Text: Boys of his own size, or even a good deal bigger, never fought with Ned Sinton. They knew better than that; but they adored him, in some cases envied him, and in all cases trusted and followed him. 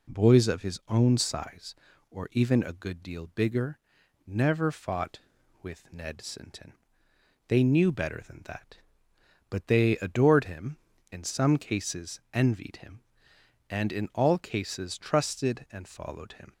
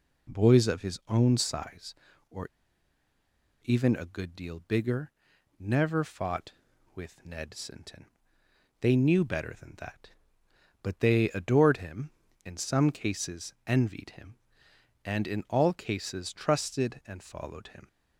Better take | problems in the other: first | pauses between "or" and "even"; at 2.4 s; 1.1 s long

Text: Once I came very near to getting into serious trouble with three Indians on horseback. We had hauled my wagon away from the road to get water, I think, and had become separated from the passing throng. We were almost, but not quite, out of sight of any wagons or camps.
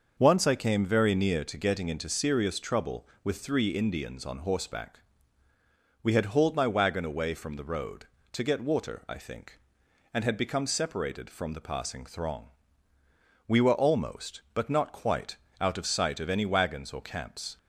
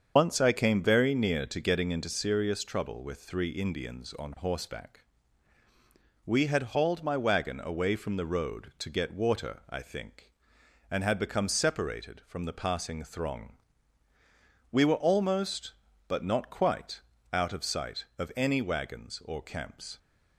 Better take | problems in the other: first | loses the start of "Once"; at 0.1 s; 85 ms // starts louder than the rest; until 1.1 s; 7 dB; also in the first

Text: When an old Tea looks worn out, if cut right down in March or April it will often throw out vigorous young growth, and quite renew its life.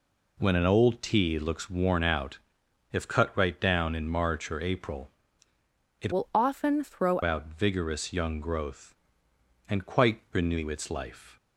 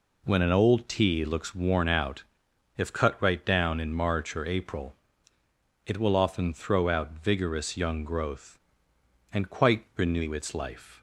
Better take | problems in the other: second | pauses between "April" and "it"; noticeable; at 5.1 s; 0.90 s long; noticeable in the second // changes voice from "will" to "throw"; from 6.1 to 7.2 s; 1.1 s long

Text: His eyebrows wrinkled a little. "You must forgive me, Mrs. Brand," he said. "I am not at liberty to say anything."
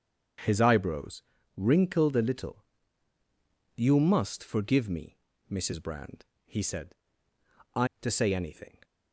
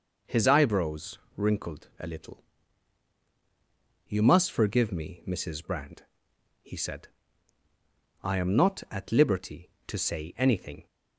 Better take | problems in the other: second | starts louder than the rest; strong; until 1.8 s; 7.5 dB // pauses between "eyebrows" and "wrinkled"; slight; at 1.2 s; 0.36 s long; slight in the second // skips "am not at liberty"; at 7.9 s

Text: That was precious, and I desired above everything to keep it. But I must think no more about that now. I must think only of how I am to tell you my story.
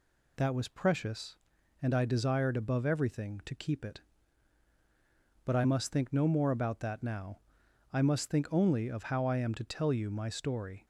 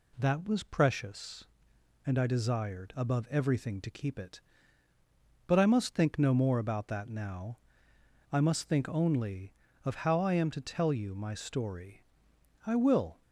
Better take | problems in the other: first | goes on to say "I will"; from 12.6 s on; 0.56 s long

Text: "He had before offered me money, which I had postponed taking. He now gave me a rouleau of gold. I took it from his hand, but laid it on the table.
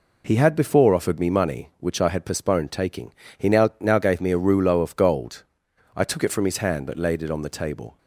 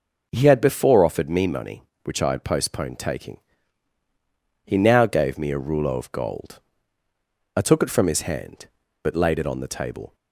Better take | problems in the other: second | says "now" twice; at 3.7 s

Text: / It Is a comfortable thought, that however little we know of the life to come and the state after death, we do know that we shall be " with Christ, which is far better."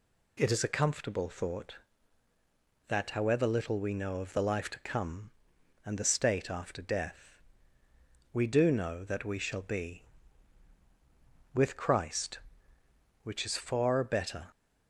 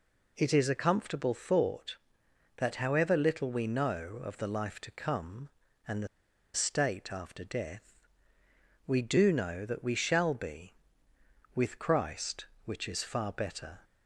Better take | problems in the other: first | pauses between "the" and "state"; noticeable; at 6.0 s; 0.46 s long

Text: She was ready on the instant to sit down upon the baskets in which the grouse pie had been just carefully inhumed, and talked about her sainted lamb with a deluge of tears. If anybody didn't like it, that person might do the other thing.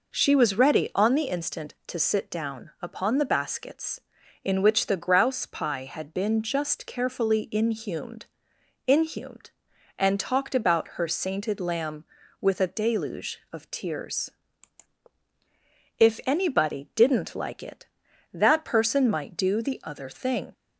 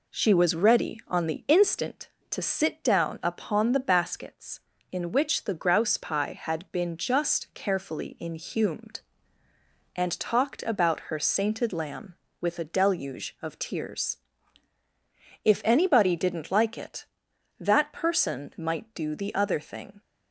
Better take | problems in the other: second | says "inhumed" twice; at 8.8 s

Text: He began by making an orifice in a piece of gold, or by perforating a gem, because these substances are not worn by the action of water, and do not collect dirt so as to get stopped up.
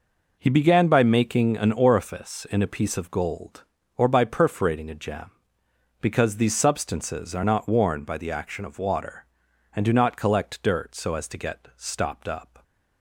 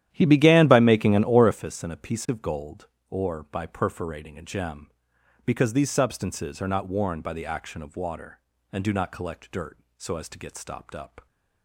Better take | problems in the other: first | starts louder than the rest; strong; until 1.6 s; 11.5 dB

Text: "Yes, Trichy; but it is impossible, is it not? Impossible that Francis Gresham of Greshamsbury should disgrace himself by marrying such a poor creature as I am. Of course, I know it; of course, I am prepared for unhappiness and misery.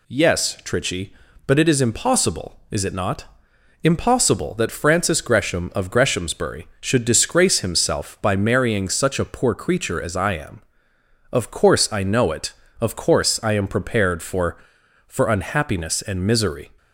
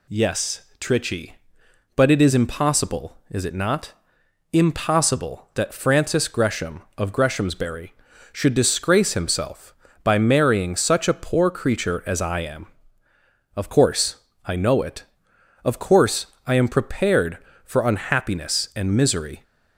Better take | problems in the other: second | says "for" twice; at 15.0 s

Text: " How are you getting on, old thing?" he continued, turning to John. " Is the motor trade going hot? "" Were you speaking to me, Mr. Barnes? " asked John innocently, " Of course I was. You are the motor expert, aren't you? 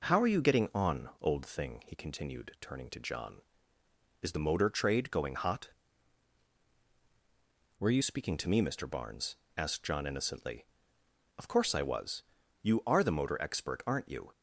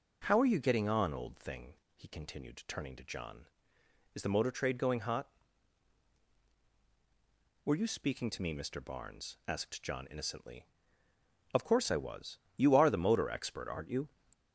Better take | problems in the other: second | starts louder than the rest; until 1.2 s; 6.5 dB; strong in the second // changes voice from "Were" to "you"; from 7.8 to 8.0 s; 0.2 s long

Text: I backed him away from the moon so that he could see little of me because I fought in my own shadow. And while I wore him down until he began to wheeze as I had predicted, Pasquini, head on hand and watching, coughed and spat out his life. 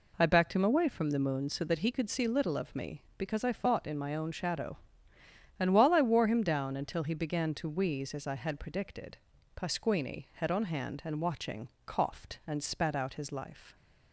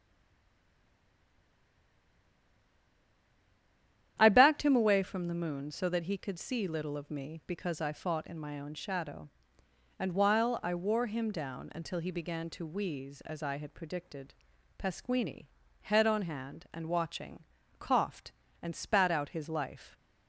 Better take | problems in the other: first | stays silent before the first word; strong; until 4.1 s; 4.1 s long // starts louder than the rest; strong; until 5.1 s; 10.5 dB

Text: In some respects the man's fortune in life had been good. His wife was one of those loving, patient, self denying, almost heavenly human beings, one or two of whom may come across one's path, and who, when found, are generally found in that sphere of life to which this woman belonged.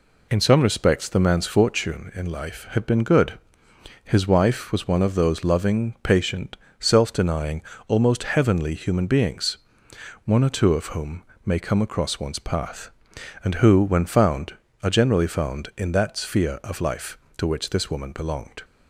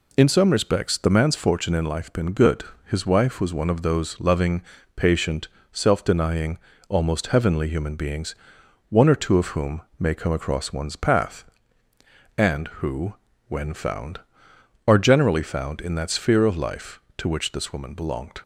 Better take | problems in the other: first | skips "had"; at 2.1 s // pauses between "whom" and "may"; slight; at 9.8 s; 0.18 s long; slight in the first

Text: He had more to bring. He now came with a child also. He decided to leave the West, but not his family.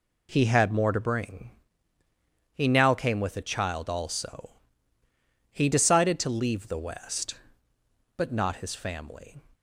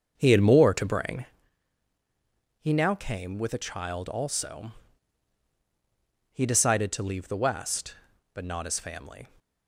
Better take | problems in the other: first | starts louder than the rest; until 1.4 s; 6.5 dB

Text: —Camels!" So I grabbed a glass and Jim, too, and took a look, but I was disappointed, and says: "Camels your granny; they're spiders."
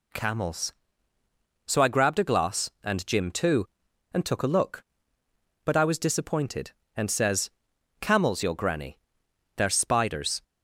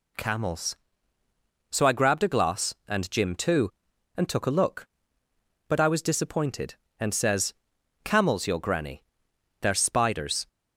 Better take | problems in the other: neither | none

